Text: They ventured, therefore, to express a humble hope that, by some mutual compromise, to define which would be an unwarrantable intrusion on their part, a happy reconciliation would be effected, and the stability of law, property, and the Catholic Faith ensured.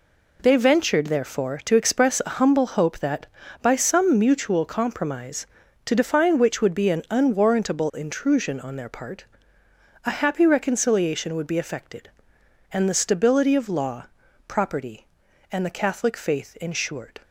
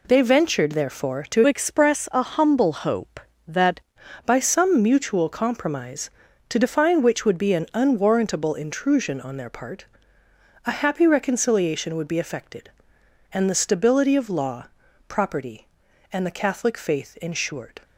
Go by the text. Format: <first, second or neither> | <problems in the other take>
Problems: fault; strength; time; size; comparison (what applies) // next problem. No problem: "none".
first | changes voice from "express" to "that"; from 1.4 to 3.8 s; 2.4 s long